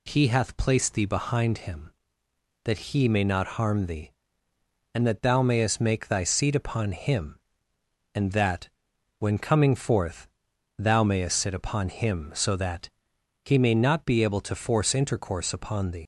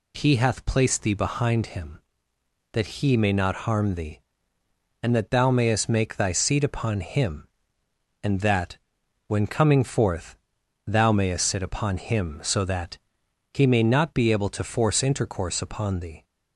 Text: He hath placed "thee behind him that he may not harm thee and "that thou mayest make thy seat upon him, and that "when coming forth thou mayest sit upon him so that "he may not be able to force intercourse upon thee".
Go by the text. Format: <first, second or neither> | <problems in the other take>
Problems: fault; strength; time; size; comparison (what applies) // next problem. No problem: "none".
second | pauses between "that" and "when"; noticeable; at 8.6 s; 0.50 s long; noticeable in the second // pauses between "forth" and "thou"; noticeable; at 10.2 s; 0.48 s long; noticeable in the second // pauses between "that" and "he"; noticeable; at 12.8 s; 0.54 s long; noticeable in the second // leaves "thee" unfinished; at 16.0 s; 95 ms